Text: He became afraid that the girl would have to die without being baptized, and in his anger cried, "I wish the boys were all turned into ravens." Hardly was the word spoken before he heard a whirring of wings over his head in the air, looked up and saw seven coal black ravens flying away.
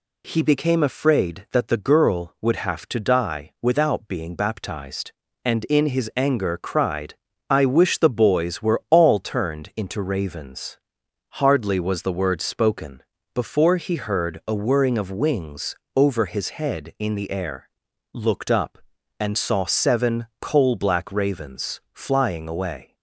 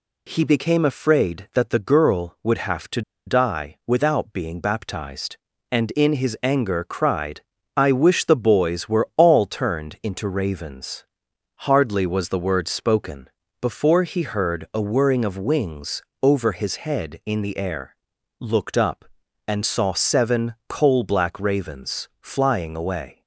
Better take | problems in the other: first | pauses between "to" and "die"; slight; at 3.0 s; 0.25 s long // pauses between "spoken" and "before"; slight; at 13.2 s; 0.32 s long; slight in the first // pauses between "wings" and "over"; slight; at 16.0 s; 0.18 s long; slight in the first

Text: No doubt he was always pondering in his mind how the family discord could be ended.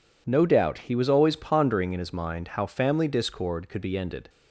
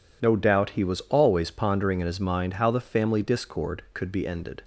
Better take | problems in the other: second | skips "the"; at 2.6 s

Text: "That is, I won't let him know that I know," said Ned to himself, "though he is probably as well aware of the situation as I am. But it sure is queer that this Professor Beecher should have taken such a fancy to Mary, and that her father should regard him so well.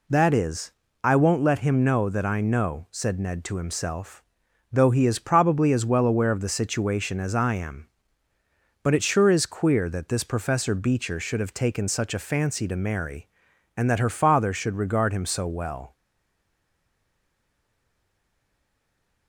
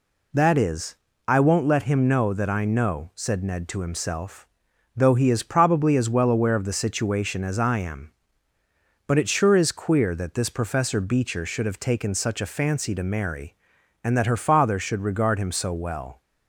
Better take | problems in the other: second | stays silent after the last word; strong; from 15.9 s on; 3.3 s long

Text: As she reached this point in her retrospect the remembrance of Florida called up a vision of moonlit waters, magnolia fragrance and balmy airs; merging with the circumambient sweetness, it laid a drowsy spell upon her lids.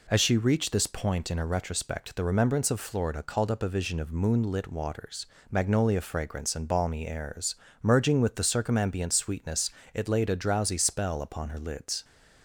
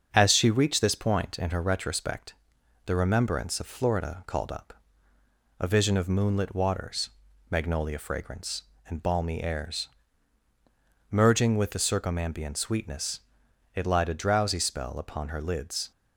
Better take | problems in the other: first | starts louder than the rest; until 1.1 s; 7 dB // pauses between "retrospect" and "the"; noticeable; at 2.3 s; 0.52 s long // pauses between "up" and "a"; noticeable; at 4.7 s; 0.88 s long // says "lied" for "laid"; at 13.8 s

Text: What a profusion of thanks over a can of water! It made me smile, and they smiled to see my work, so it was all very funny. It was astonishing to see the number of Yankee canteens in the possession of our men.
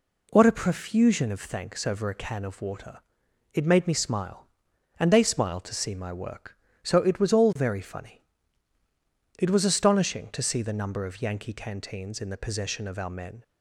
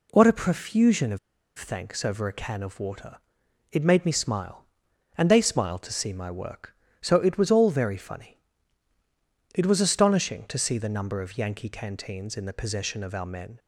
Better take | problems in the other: first | pauses between "of" and "thanks"; at 1.1 s; 0.39 s long

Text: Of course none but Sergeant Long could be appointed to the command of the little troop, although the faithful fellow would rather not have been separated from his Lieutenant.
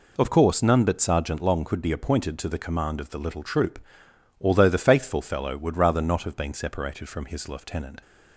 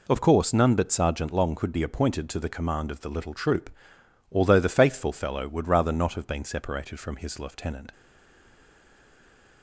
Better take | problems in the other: first | stays silent after the last word; noticeable; from 7.9 s on; 1.7 s long

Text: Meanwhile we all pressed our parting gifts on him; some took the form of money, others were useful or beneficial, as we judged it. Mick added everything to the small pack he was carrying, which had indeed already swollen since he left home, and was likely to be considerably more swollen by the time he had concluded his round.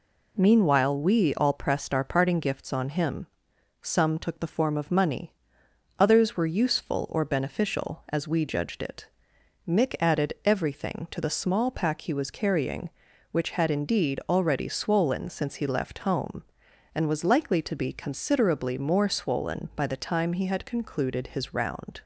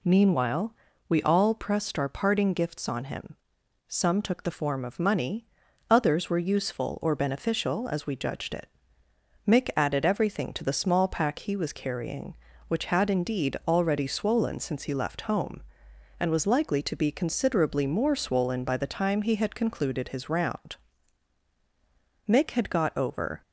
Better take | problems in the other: first | pauses between "Meanwhile" and "we"; slight; at 0.7 s; 0.34 s long // goes on to say "Mick had got over"; noticeable; from 22.2 s on; 1.1 s long

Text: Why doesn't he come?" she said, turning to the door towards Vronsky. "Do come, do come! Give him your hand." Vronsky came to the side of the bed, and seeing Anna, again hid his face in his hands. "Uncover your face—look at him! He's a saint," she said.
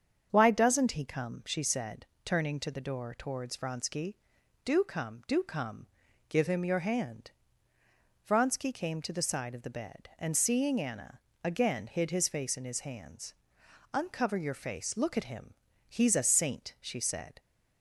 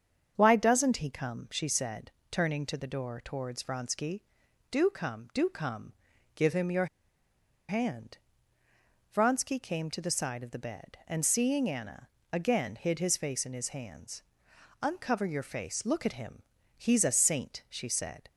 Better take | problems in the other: first | starts louder than the rest; strong; until 1.3 s; 7 dB; also in the first // pauses between "your" and "hand"; noticeable; at 6.8 s; 0.81 s long

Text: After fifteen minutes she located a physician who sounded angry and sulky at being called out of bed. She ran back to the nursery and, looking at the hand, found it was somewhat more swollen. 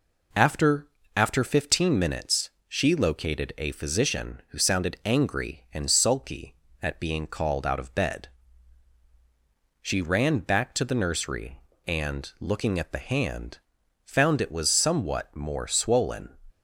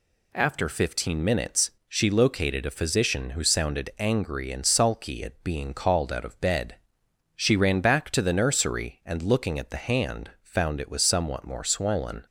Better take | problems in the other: second | says "After" twice; at 1.1 s // pauses between "minutes" and "she"; slight; at 2.4 s; 0.18 s long; slight in the second

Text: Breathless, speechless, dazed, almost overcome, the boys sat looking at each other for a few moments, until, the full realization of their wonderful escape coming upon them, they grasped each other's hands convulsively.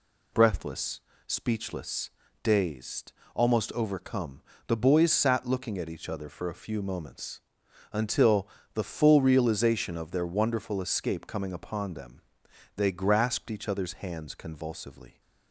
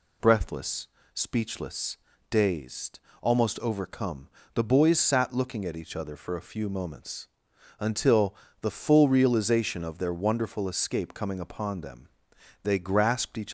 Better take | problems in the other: first | stops before "other's hands convulsively"; at 13.4 s

